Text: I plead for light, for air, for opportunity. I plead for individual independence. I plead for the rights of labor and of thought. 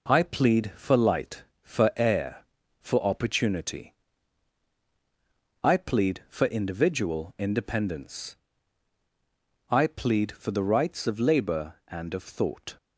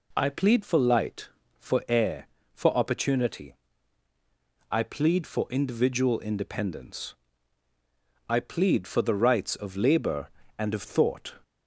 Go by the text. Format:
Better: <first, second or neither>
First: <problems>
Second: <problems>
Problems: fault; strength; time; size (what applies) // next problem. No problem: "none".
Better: neither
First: none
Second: none